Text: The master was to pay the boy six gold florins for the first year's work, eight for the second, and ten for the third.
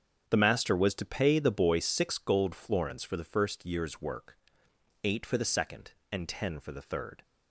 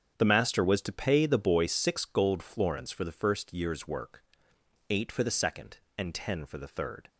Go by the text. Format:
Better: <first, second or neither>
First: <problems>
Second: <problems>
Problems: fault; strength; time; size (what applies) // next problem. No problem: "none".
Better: neither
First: starts louder than the rest; strong; until 1.2 s; 7.5 dB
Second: starts louder than the rest; strong; until 1.1 s; 7.5 dB